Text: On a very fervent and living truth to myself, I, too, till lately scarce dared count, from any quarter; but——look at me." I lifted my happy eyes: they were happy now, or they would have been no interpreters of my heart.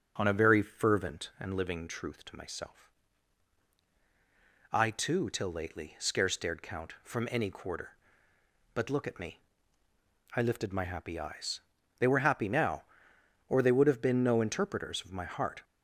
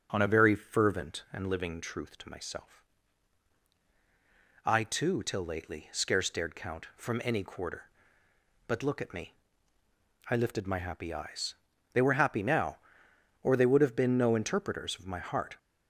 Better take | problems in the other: neither | starts louder than the rest; the same in both

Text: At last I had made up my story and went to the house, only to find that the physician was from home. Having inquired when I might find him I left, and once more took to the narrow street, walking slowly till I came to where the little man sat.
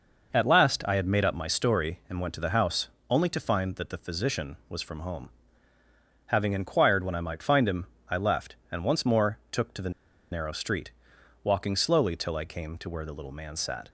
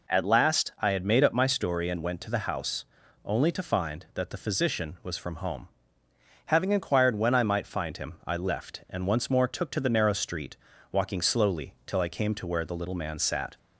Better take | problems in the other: second | pauses between "him" and "I"; slight; at 7.8 s; 0.22 s long // pauses between "the" and "narrow"; at 9.9 s; 0.41 s long

